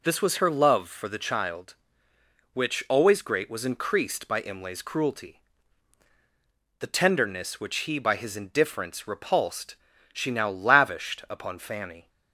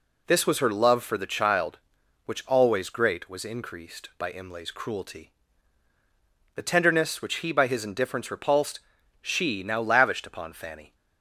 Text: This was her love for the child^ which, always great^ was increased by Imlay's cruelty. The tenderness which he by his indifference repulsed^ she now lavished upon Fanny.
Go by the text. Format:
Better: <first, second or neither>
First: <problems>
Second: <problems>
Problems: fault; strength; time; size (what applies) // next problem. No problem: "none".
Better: neither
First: pauses between "repulsed" and "she"; slight; at 9.7 s; 0.36 s long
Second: pauses between "repulsed" and "she"; at 8.7 s; 0.42 s long